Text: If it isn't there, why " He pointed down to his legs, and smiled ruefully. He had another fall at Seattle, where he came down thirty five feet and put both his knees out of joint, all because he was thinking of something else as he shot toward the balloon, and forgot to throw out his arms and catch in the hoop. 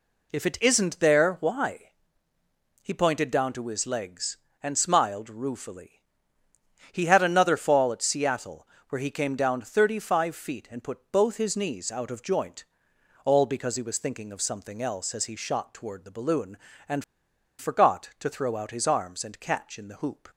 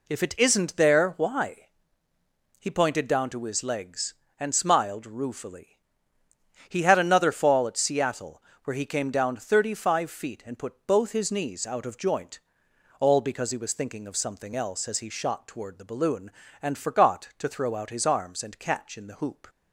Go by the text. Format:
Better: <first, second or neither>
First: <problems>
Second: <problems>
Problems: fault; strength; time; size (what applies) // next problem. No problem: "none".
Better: second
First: pauses between "and" and "forgot"; noticeable; at 17.0 s; 0.56 s long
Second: none